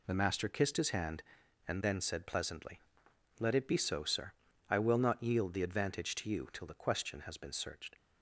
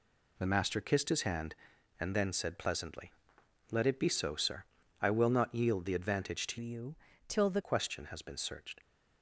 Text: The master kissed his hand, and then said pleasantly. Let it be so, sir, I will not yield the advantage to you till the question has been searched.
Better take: first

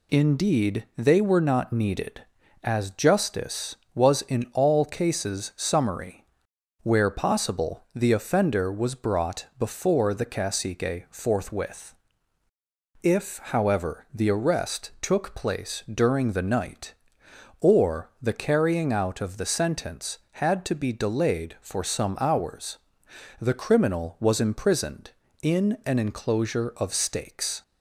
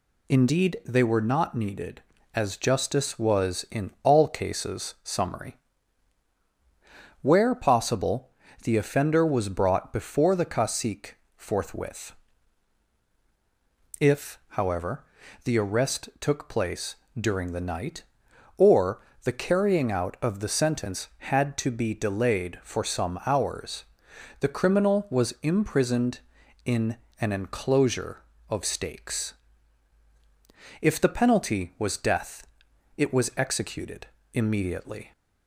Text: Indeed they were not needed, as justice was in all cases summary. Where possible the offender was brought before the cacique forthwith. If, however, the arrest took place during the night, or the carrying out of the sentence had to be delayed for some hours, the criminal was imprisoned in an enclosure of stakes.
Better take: first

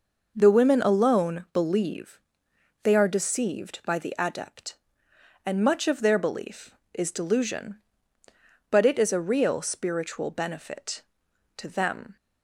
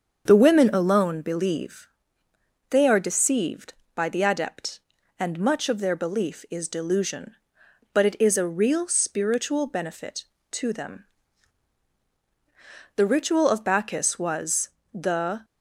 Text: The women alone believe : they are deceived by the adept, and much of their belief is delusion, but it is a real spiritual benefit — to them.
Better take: first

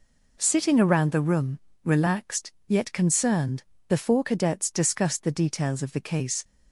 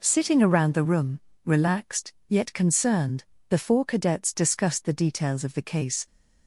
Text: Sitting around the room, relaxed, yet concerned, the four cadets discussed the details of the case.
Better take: neither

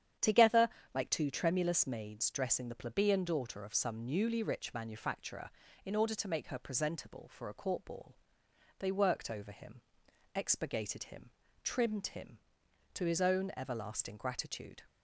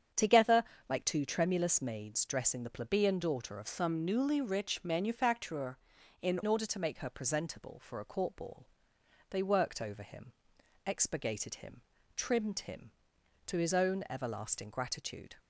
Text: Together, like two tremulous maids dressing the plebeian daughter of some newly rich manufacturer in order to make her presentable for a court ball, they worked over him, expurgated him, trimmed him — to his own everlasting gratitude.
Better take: first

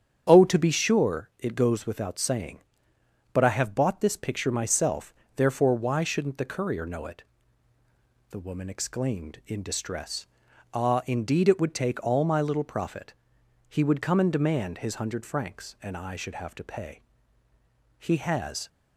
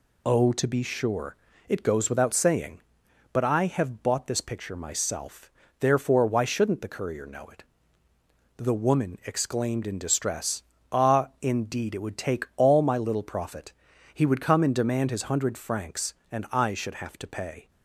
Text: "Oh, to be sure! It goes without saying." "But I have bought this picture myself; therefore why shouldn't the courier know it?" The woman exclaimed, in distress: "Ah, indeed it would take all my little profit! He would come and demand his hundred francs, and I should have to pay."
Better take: second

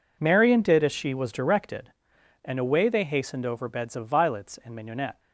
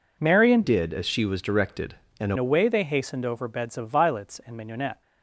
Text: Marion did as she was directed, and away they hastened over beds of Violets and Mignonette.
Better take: first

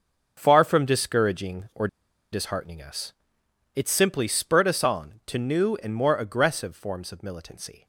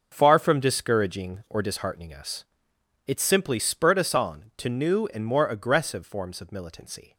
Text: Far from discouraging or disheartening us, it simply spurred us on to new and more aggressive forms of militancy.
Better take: second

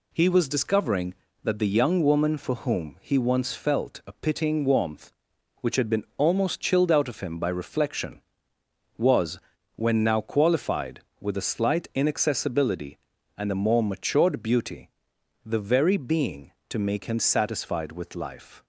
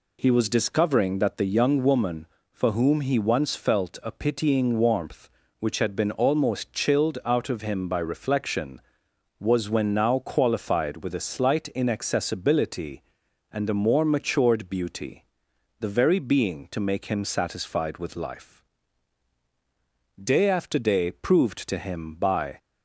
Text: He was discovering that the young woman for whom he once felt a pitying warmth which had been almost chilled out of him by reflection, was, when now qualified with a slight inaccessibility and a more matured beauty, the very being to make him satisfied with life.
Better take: first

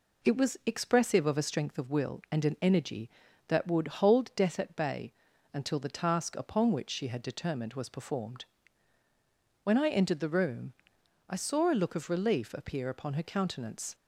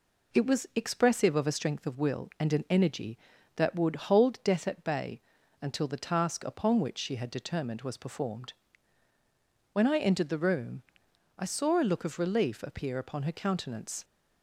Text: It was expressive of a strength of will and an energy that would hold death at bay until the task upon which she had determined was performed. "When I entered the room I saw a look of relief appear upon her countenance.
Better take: neither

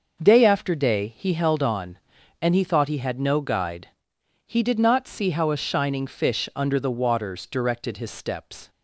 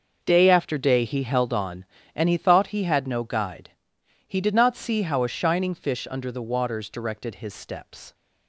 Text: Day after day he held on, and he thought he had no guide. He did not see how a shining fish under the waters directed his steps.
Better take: neither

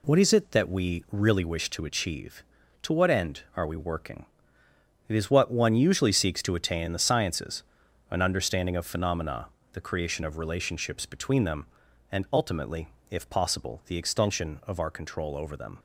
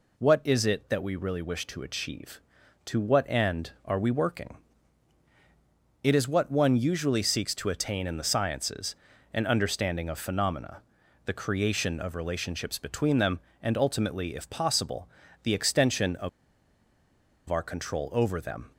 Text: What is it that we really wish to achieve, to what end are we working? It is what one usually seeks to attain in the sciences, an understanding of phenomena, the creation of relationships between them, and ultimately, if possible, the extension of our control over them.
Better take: first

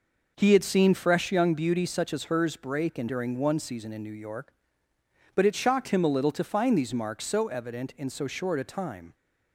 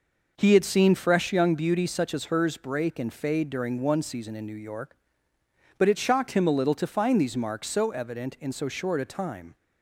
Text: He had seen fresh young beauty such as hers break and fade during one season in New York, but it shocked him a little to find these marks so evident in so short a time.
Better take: second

